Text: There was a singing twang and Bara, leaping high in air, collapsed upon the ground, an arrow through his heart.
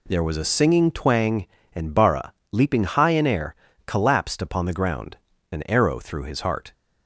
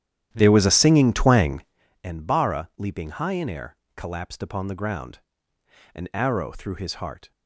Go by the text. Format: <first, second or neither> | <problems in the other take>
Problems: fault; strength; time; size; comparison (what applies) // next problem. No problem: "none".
first | starts louder than the rest; strong; until 1.8 s; 11 dB